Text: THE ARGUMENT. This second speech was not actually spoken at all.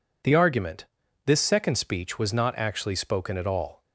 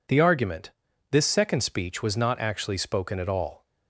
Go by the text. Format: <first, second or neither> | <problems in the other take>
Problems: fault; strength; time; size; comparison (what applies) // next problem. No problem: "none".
neither | none